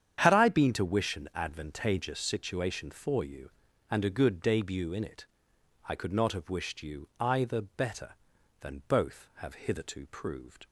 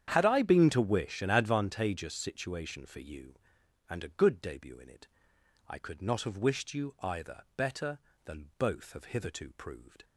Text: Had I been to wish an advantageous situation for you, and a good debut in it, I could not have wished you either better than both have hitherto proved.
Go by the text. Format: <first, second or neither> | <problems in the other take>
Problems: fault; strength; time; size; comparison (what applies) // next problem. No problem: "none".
neither | starts louder than the rest; strong; the same in both